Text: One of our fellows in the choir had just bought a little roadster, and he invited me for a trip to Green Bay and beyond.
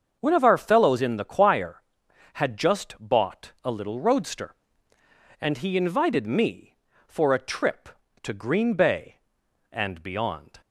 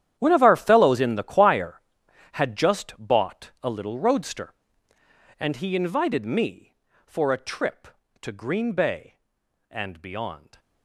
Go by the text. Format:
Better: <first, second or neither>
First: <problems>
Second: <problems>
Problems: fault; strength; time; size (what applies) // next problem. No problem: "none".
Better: first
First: starts louder than the rest; until 1.2 s; 6.5 dB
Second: gets quieter; strong; throughout; 16 dB // starts louder than the rest; strong; until 1.2 s; 10.5 dB